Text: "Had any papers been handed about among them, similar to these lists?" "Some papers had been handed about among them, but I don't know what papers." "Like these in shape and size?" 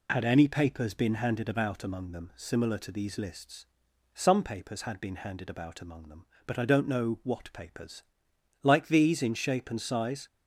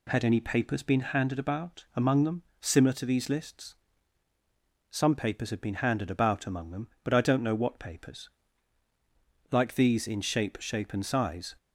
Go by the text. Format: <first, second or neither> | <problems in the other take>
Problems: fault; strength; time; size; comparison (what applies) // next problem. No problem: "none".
first | says "shape" twice; at 10.6 s